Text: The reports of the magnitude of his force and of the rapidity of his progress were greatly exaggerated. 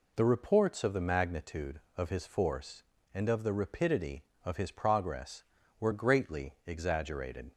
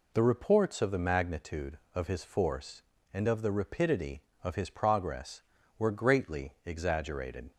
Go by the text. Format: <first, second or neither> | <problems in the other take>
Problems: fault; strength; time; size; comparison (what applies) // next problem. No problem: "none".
neither | none